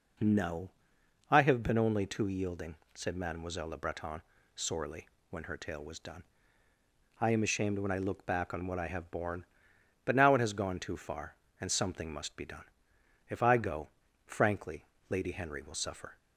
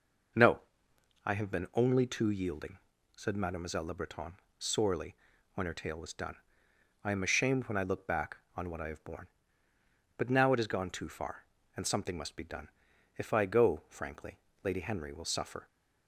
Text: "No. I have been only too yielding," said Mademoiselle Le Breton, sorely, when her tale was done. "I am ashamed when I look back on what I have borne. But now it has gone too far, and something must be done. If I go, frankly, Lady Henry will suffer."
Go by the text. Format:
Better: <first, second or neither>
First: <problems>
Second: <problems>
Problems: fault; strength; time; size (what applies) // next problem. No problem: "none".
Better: neither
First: none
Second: none